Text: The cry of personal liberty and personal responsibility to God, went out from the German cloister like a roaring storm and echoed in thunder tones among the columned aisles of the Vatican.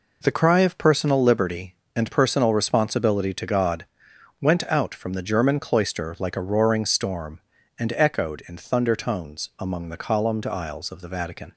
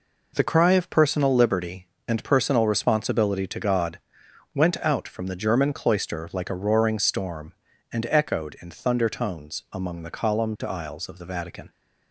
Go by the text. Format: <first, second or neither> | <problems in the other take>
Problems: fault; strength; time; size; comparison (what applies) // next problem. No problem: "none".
neither | none